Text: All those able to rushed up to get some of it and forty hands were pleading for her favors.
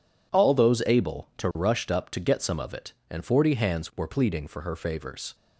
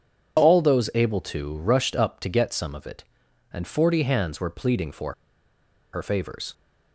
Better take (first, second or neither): first